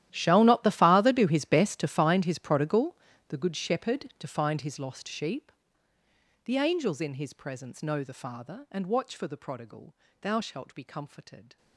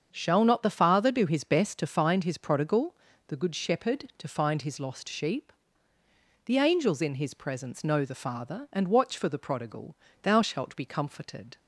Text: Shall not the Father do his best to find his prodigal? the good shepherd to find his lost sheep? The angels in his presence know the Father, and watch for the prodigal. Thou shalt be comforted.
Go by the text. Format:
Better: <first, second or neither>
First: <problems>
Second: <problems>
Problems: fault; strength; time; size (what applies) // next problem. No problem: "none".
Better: second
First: gets quieter; strong; throughout; 19.5 dB // starts louder than the rest; strong; until 1.1 s; 12.5 dB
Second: starts louder than the rest; strong; until 1.1 s; 7 dB